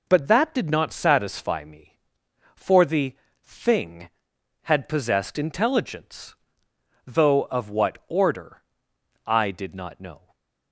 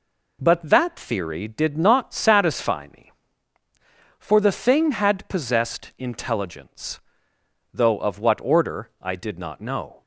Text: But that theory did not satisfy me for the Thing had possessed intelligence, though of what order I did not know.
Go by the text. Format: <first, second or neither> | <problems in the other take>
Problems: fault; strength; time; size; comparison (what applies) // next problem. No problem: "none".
second | skips "theory"; at 0.5 s // pauses between "the" and "Thing"; slight; at 3.1 s; 0.34 s long // pauses between "order" and "I"; noticeable; at 8.6 s; 0.64 s long // stays silent after the last word; slight; from 10.1 s on; 0.6 s long